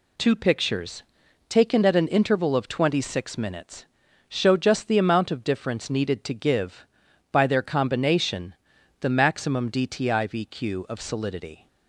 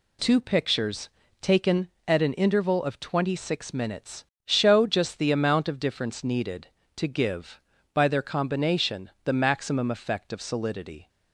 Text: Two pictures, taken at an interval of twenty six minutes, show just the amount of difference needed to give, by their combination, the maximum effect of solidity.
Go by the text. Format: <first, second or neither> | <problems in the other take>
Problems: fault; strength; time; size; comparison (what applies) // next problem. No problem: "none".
second | says "dtivq" for "effect"; at 9.7 s